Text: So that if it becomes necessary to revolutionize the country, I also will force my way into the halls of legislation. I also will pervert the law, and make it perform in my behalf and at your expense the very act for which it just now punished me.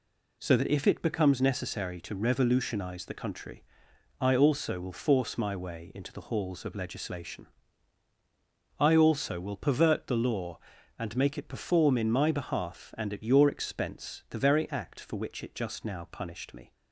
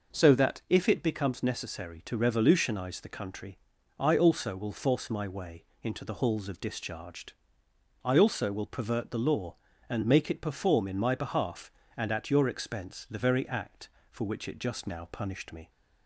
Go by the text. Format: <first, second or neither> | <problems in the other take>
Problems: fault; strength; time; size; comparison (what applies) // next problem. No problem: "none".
first | pauses between "way" and "into"; slight; at 5.6 s; 0.18 s long // says "discharged" for "legislation"; at 6.6 s